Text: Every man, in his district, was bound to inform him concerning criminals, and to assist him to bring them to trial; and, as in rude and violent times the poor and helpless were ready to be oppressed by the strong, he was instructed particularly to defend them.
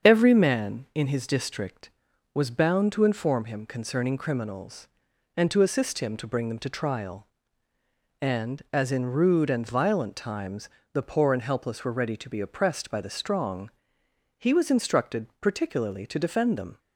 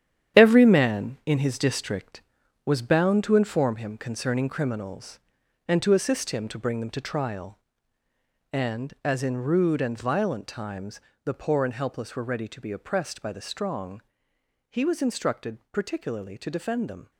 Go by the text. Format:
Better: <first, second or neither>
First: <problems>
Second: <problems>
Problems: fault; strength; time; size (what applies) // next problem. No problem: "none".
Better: first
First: starts louder than the rest; until 1.1 s; 7 dB // pauses between "times" and "the"; slight; at 10.6 s; 0.24 s long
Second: gets quieter; strong; throughout; 9.5 dB // starts louder than the rest; strong; until 1.4 s; 9.5 dB // pauses between "times" and "the"; slight; at 10.9 s; 0.24 s long